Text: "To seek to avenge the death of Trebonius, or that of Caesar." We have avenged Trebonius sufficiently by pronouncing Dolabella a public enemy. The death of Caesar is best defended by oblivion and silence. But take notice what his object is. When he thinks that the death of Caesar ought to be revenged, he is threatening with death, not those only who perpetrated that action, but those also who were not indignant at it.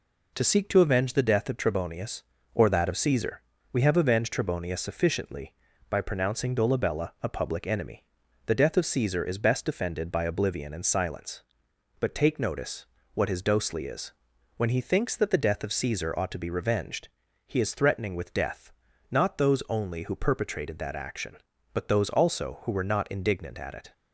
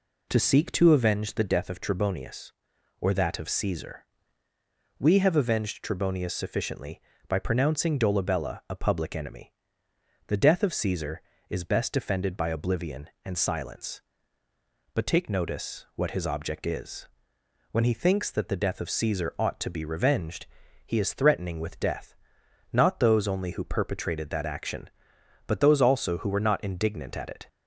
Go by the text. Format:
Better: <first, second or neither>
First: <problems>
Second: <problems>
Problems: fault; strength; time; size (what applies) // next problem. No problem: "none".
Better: second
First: pauses between "notice" and "what"; slight; at 12.8 s; 0.26 s long // says "dosely" for "object"; at 13.4 s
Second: none